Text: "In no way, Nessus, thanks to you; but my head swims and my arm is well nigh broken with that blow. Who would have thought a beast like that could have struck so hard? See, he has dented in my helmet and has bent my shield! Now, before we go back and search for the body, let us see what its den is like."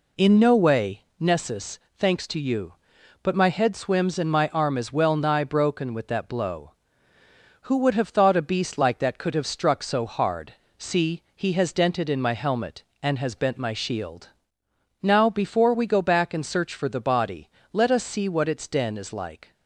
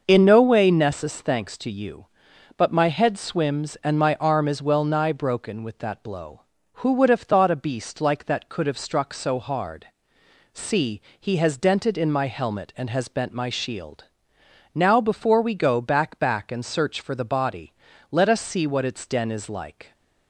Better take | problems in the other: first | starts louder than the rest; noticeable; until 1.0 s; 6 dB // says "back" twice; at 16.1 s

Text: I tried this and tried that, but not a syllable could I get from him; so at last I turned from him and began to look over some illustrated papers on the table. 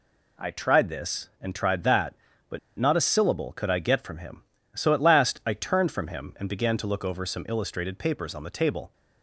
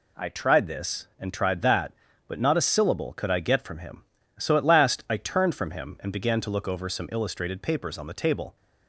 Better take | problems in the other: second | pauses between "but" and "not"; slight; at 2.5 s; 0.19 s long

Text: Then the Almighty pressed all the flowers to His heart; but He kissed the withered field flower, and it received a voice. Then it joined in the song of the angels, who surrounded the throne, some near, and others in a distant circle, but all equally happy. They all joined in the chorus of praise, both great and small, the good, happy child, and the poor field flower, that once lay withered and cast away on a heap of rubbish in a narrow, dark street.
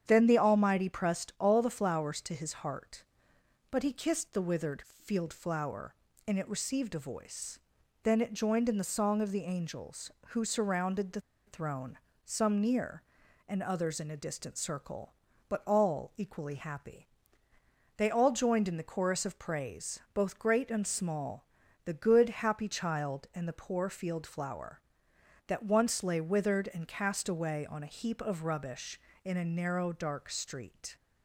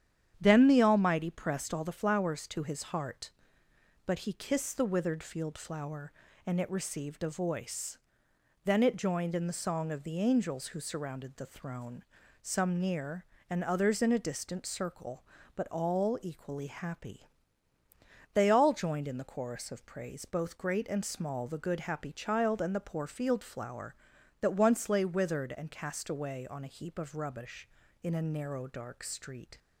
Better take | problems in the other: second | starts louder than the rest; strong; until 1.0 s; 8.5 dB; strong in the second // pauses between "withered" and "field"; slight; at 4.8 s; 0.18 s long // pauses between "the" and "throne"; slight; at 11.2 s; 0.26 s long

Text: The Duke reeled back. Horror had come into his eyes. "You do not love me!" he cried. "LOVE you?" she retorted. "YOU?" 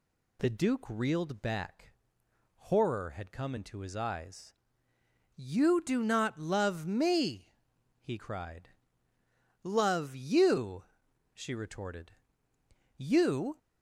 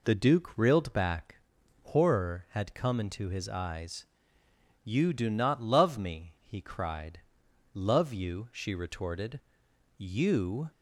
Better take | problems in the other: neither | none

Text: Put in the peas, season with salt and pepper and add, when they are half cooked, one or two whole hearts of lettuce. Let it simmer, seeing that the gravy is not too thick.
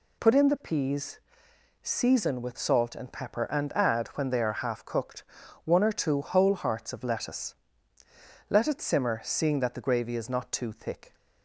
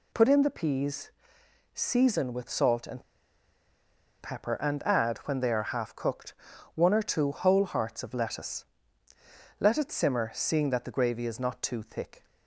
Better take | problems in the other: first | pauses between "and" and "pepper"; at 3.0 s; 1.1 s long

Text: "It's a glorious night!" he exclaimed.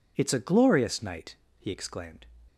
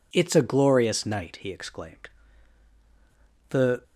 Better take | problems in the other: first | goes on to say "The"; slight; from 3.4 s on; 0.34 s long

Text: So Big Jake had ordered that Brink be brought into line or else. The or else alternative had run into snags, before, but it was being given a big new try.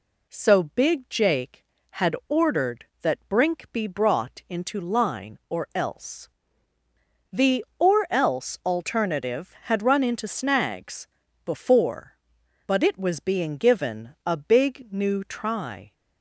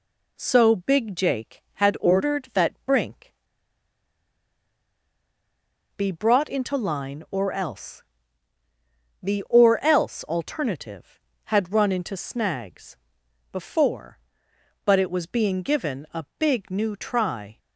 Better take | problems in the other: first | pauses between "Brink" and "be"; strong; at 3.3 s; 2.6 s long

